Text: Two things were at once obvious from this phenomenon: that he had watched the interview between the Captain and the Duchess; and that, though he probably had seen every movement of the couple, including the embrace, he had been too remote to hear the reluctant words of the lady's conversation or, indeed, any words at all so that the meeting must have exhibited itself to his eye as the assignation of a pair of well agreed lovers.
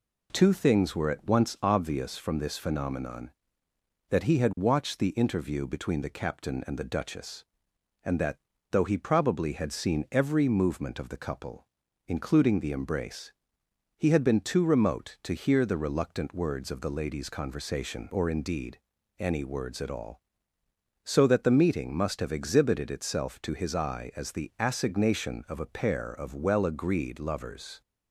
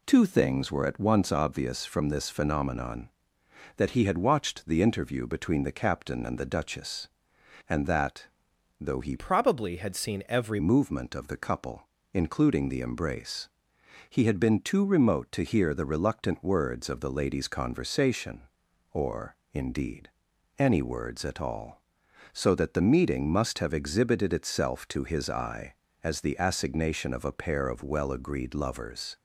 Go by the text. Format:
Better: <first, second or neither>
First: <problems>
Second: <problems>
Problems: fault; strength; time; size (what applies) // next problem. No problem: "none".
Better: first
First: none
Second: changes voice from "probably" to "every"; from 9.1 to 10.6 s; 1.5 s long